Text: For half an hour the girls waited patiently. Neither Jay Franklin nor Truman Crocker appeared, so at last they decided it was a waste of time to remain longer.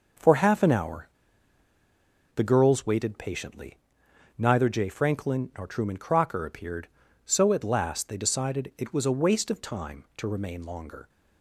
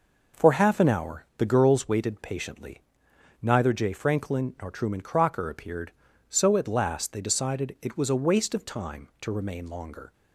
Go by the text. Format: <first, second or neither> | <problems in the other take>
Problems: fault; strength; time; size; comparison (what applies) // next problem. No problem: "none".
second | pauses between "hour" and "the"; strong; at 1.0 s; 1.2 s long